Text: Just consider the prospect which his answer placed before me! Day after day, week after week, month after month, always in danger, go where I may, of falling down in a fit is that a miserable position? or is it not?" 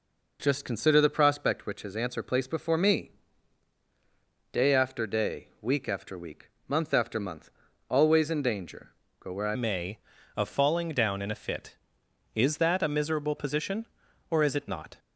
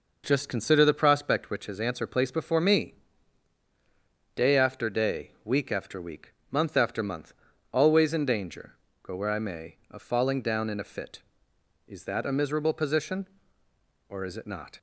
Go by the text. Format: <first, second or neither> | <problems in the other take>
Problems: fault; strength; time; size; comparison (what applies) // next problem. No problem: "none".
second | changes voice at "may"; from 9.5 s on; 5.4 s long